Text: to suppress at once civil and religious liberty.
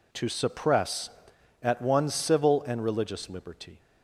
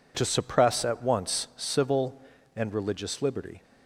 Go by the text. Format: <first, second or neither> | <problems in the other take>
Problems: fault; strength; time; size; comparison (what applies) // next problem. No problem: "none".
second | says "one" for "once"; at 1.8 s